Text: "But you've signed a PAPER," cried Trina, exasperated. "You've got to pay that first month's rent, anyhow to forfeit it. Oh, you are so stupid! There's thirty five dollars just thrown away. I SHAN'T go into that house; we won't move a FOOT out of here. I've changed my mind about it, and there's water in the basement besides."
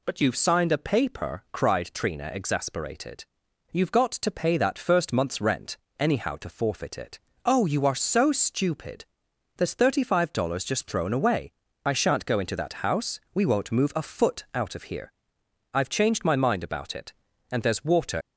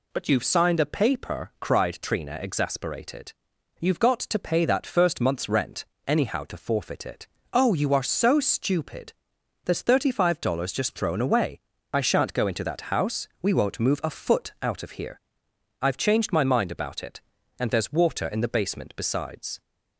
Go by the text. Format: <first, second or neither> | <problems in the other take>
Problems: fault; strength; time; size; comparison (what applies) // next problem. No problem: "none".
second | stops before "in the basement besides"; at 18.2 s